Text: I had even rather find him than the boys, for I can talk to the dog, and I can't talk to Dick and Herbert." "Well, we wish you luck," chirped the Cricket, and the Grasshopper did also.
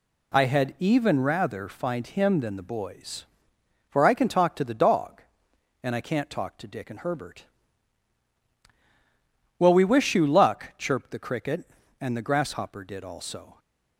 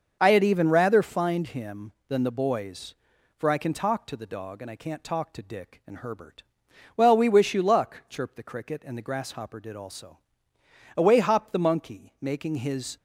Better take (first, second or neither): first